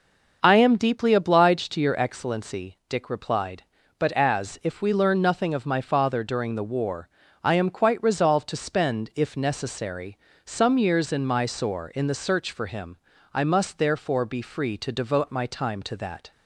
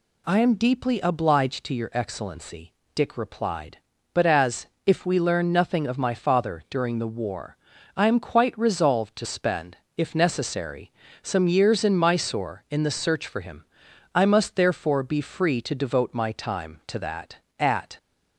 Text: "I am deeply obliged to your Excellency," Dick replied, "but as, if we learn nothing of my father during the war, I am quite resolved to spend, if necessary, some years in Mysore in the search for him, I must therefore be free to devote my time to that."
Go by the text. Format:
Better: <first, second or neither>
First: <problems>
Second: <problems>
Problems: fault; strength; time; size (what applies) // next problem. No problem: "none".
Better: first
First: none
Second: goes on to say "At"; slight; from 17.5 s on; 0.38 s long